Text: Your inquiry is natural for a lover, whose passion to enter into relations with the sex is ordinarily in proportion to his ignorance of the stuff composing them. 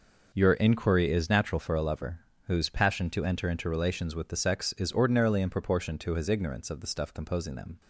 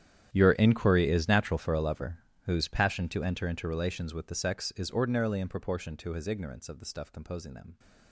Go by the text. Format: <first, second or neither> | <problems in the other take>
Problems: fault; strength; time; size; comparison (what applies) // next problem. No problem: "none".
first | gets quieter; strong; throughout; 19 dB